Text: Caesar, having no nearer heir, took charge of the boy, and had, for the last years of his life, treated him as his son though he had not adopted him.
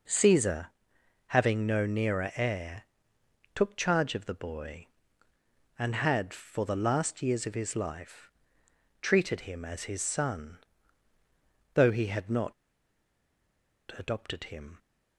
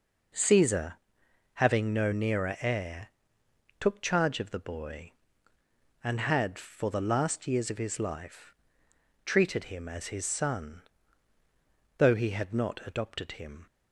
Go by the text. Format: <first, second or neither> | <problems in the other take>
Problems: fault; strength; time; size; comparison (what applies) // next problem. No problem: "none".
second | pauses between "son" and "though"; at 10.5 s; 1.1 s long; also in the second // pauses between "not" and "adopted"; strong; at 12.5 s; 1.4 s long